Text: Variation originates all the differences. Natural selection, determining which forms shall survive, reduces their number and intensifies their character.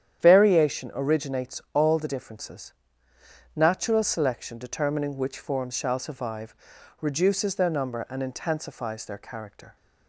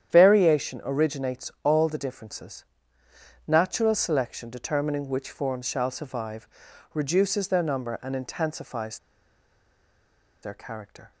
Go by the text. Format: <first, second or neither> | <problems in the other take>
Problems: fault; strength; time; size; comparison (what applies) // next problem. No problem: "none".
first | starts louder than the rest; strong; until 1.1 s; 9.5 dB; strong in the first // pauses between "intensifies" and "their"; strong; at 8.9 s; 1.4 s long